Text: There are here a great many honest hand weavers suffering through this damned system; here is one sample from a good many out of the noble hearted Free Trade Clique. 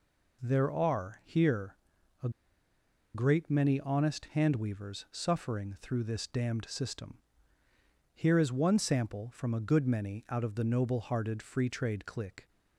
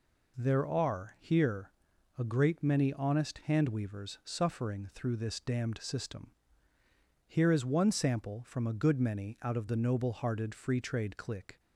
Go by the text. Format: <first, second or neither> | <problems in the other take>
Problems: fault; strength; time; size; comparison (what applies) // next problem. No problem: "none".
second | pauses between "here" and "a"; noticeable; at 1.7 s; 0.48 s long; noticeable in the second // pauses between "a" and "great"; noticeable; at 2.2 s; 0.85 s long